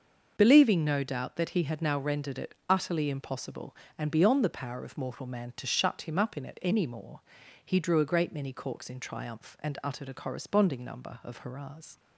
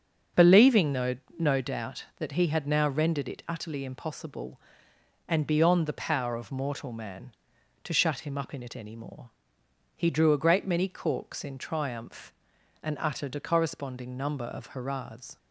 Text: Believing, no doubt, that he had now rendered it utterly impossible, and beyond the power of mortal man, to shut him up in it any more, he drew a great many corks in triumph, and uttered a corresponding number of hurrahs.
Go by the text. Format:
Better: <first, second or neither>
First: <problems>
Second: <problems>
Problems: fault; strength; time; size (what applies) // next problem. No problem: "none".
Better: first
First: starts louder than the rest; noticeable; until 1.3 s; 6 dB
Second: starts louder than the rest; until 1.5 s; 6.5 dB // says "no" twice; at 1.3 s